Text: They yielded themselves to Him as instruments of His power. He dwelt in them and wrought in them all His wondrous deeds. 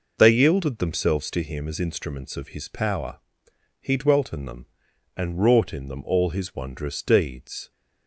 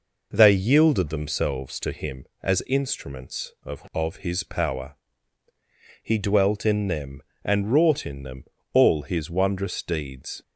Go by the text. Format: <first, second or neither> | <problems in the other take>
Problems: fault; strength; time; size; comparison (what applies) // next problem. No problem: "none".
first | says "of" twice; at 3.9 s // pauses between "them" and "all"; slight; at 8.4 s; 0.28 s long